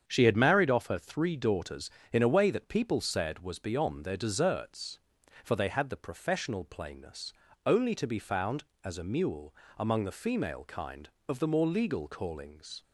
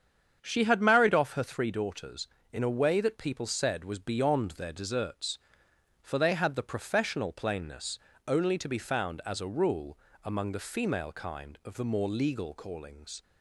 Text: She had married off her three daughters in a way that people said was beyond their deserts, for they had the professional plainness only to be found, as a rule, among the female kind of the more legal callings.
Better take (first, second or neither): second